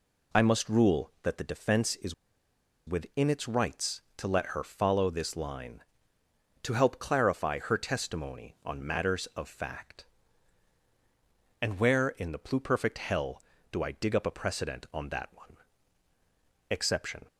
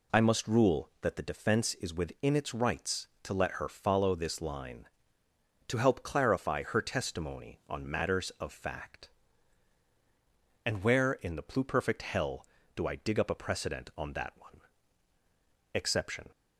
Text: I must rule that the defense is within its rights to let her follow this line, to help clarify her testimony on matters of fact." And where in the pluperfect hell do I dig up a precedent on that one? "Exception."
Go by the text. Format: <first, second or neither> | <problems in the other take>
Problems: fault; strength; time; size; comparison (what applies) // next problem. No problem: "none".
second | pauses between "is" and "within"; noticeable; at 2.1 s; 0.73 s long